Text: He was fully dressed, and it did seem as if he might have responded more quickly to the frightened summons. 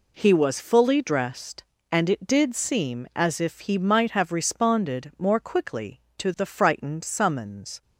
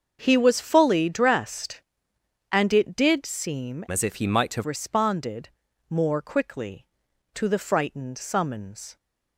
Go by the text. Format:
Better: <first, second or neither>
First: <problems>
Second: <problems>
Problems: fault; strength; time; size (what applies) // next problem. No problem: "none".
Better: first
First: none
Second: starts louder than the rest; until 1.2 s; 6.5 dB // changes voice from "as" to "have"; from 3.9 to 4.6 s; 0.7 s long // pauses between "responded" and "more"; at 5.4 s; 0.38 s long